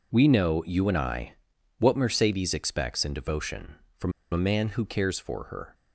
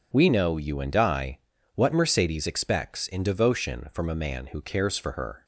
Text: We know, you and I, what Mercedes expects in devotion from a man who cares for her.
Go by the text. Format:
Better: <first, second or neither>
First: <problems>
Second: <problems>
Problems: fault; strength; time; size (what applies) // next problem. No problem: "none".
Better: second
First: pauses between "from" and "a"; slight; at 4.1 s; 0.20 s long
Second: none